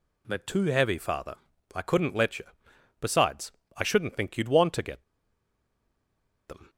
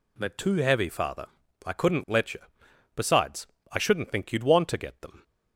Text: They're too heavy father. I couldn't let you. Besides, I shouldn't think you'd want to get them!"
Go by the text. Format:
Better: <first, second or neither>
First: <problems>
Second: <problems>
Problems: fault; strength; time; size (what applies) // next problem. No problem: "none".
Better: second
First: pauses between "get" and "them"; strong; at 5.0 s; 1.4 s long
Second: none